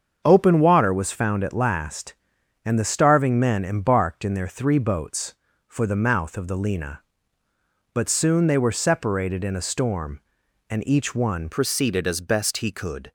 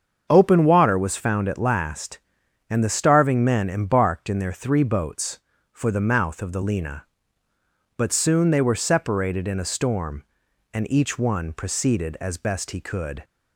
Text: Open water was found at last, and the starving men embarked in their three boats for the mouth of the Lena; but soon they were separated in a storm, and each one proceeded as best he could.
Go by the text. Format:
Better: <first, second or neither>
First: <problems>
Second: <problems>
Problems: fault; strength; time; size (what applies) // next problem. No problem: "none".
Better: second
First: starts louder than the rest; until 1.2 s; 7 dB // changes voice at "proceeded"; from 11.5 s on; 1.6 s long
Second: starts louder than the rest; until 1.3 s; 7 dB